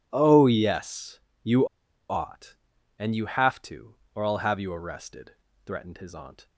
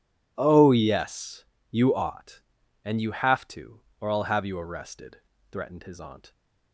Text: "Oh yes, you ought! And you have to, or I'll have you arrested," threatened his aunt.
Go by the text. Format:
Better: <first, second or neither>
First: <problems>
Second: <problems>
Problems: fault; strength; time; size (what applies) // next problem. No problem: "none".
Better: second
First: pauses between "you" and "ought"; at 1.6 s; 0.42 s long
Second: none